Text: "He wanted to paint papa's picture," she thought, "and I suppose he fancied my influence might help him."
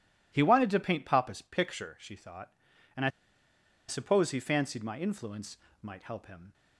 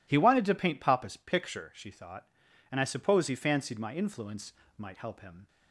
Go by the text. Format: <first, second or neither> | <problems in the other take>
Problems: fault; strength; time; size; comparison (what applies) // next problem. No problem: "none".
second | pauses between "I" and "suppose"; noticeable; at 3.0 s; 0.78 s long // pauses between "influence" and "might"; slight; at 5.5 s; 0.24 s long; slight in the second